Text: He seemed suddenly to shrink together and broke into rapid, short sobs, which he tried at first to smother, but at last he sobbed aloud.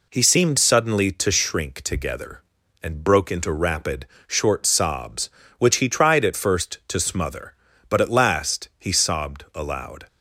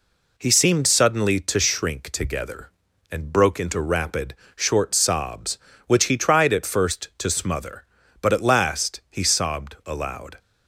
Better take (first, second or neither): neither